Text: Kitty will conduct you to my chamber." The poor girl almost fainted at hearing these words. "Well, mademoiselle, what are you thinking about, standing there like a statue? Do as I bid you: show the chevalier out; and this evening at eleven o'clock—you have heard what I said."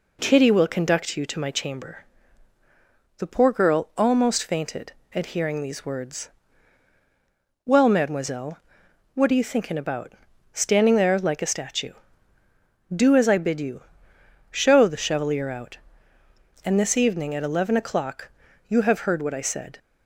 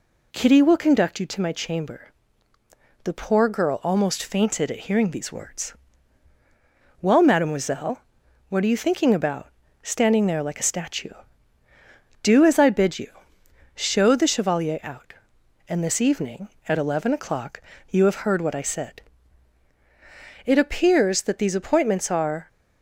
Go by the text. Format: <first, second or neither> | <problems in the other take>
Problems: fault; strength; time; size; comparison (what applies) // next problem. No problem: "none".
first | goes on to say "It appears that these appointments are"; strong; from 20.4 s on; 2.0 s long